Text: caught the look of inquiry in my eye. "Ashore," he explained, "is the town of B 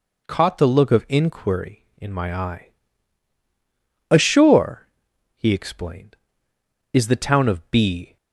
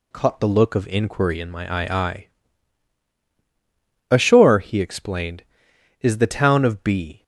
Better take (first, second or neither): first